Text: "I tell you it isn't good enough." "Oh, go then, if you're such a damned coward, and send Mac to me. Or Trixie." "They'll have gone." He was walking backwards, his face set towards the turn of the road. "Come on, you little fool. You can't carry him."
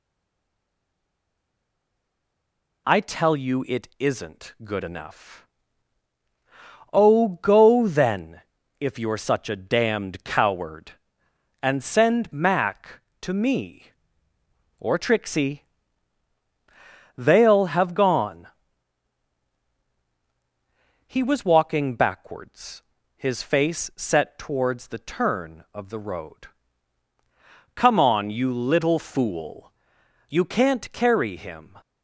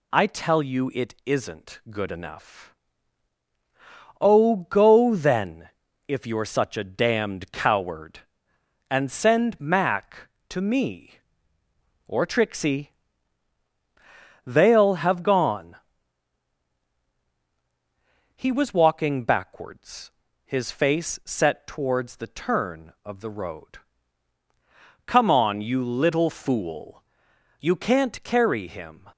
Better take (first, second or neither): second